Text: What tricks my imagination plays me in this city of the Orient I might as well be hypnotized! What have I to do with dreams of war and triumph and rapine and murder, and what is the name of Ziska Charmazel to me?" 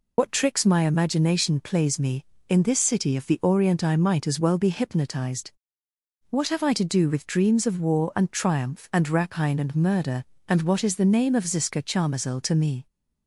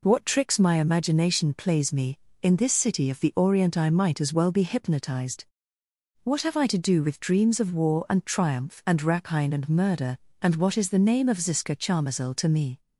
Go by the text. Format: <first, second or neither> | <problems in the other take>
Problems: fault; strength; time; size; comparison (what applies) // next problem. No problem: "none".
second | loses the start of "What"; at 0.1 s; 90 ms